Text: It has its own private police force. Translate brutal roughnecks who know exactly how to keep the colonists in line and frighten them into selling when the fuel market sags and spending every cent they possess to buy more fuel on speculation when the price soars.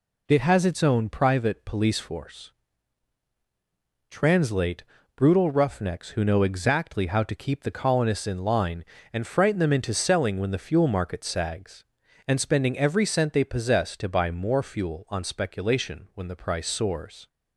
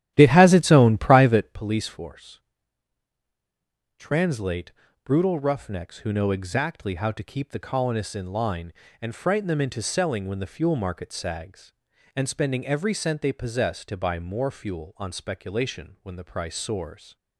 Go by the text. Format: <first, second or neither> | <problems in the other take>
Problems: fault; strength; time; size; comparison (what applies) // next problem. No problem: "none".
first | starts louder than the rest; strong; until 1.6 s; 12 dB // pauses between "Translate" and "brutal"; slight; at 4.7 s; 0.32 s long; slight in the first